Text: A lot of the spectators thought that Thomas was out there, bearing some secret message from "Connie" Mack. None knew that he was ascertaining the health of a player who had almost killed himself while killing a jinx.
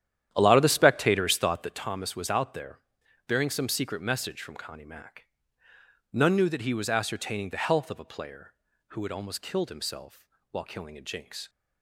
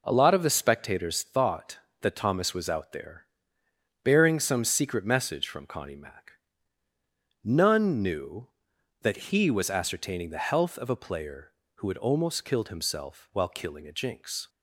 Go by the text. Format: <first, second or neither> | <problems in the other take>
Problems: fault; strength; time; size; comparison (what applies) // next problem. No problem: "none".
second | starts louder than the rest; strong; until 1.9 s; 10.5 dB // pauses between "himself" and "while"; slight; at 10.2 s; 0.24 s long